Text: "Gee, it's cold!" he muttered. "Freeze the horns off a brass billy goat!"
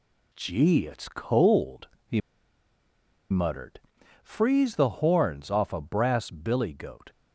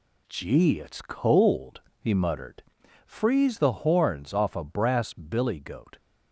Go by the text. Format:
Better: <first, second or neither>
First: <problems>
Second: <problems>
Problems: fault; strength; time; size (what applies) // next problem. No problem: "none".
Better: second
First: pauses between "he" and "muttered"; at 2.2 s; 1.1 s long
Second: none